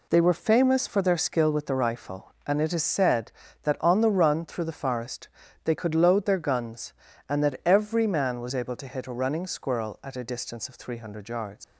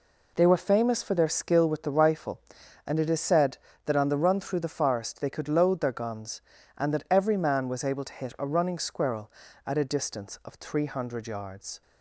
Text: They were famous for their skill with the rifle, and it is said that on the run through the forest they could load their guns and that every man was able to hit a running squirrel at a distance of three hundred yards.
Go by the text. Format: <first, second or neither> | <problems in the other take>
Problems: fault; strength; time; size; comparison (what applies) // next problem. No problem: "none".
second | pauses between "forest" and "they"; slight; at 5.2 s; 0.36 s long // leaves "yards" unfinished; at 11.6 s; 115 ms